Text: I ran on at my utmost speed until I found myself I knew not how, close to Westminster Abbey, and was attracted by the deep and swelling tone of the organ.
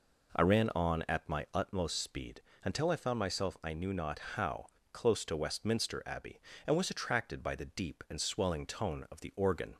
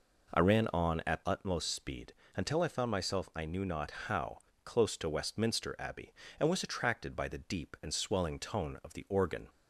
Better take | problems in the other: first | skips "my"; at 1.2 s // pauses between "speed" and "until"; slight; at 2.1 s; 0.22 s long; slight in the first // pauses between "not" and "how"; slight; at 3.9 s; 0.16 s long; slight in the first

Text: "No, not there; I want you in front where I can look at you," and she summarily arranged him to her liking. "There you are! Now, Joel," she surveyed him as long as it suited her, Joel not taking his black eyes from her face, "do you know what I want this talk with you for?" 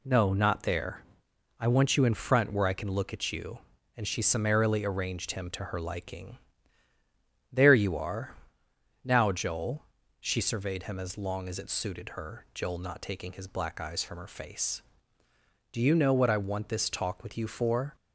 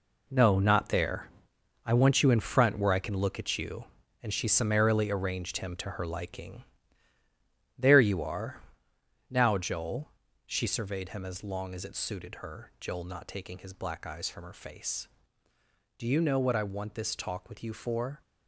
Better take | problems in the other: first | gets quieter; strong; throughout; 10 dB

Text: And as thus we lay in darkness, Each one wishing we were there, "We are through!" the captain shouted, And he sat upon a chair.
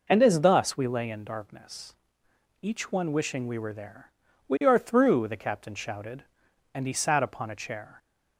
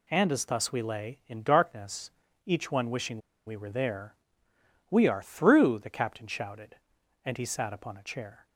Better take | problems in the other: first | pauses between "wishing" and "we"; slight; at 3.1 s; 0.27 s long

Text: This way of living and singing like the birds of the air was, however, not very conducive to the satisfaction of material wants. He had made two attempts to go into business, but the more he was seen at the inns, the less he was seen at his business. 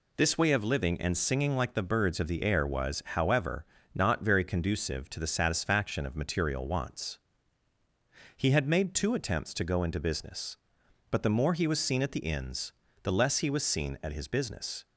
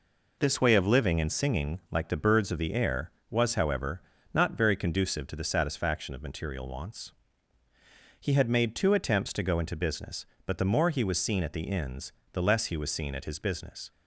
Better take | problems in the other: neither | none

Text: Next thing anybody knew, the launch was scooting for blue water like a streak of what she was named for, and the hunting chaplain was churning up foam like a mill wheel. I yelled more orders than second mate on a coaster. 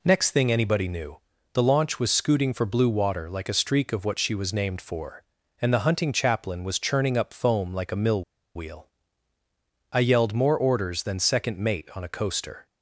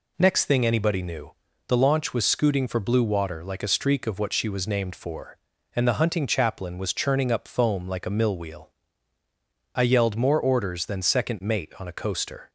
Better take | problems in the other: second | pauses between "mill" and "wheel"; slight; at 8.2 s; 0.33 s long

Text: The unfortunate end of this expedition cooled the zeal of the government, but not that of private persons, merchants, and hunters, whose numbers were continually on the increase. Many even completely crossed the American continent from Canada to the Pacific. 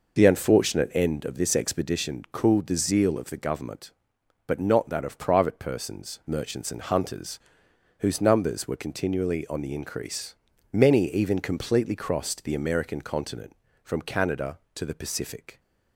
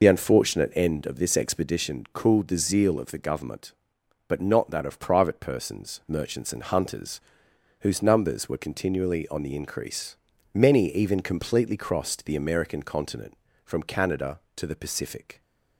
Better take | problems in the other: first | loses the start of "The"; at 0.0 s; 40 ms

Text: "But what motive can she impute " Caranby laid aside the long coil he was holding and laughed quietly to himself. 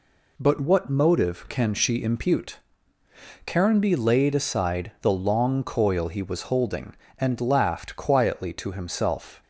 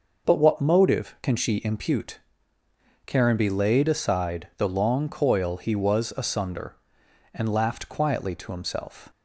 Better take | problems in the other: first | says "asunder" for "holding"; at 6.1 s

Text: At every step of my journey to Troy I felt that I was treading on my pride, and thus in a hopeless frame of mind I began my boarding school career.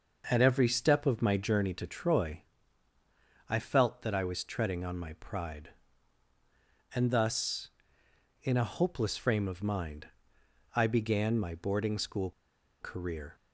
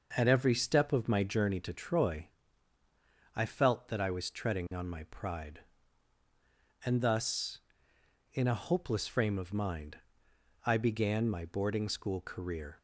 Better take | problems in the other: second | pauses between "Troy" and "I"; at 2.4 s; 1.0 s long; also in the second // pauses between "mind" and "I"; noticeable; at 10.0 s; 0.68 s long; noticeable in the second // pauses between "school" and "career"; noticeable; at 12.3 s; 0.50 s long

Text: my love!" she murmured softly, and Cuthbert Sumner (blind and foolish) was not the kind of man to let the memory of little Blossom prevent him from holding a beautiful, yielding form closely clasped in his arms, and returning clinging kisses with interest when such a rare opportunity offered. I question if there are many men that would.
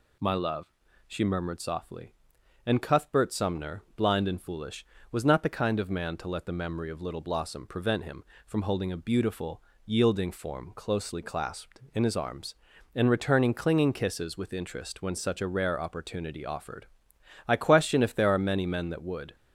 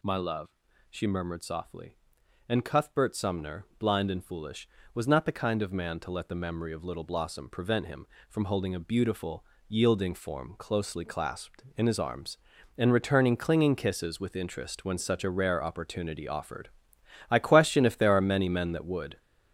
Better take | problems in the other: first | gets louder; throughout; 6 dB

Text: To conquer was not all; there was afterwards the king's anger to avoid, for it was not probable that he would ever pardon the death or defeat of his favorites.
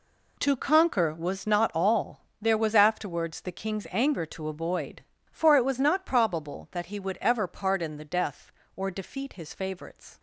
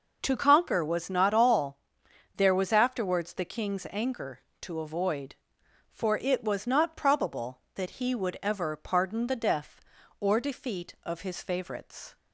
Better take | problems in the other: second | skips "of"; at 9.3 s

